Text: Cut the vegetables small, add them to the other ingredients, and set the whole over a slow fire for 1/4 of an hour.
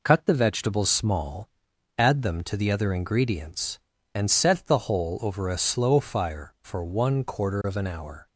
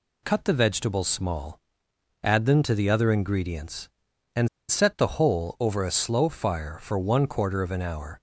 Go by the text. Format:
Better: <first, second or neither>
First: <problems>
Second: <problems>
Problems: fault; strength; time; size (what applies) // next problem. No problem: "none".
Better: first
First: none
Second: pauses between "and" and "set"; slight; at 4.4 s; 0.22 s long